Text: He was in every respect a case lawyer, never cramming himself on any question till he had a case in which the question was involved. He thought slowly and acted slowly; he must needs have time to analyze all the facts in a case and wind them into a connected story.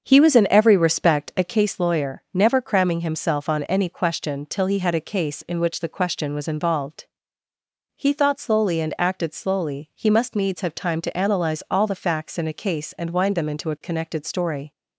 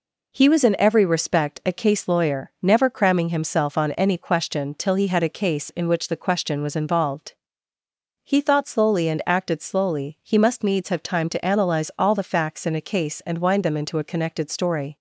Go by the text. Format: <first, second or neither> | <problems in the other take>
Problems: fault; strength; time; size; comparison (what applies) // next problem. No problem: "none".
second | starts louder than the rest; until 1.6 s; 7 dB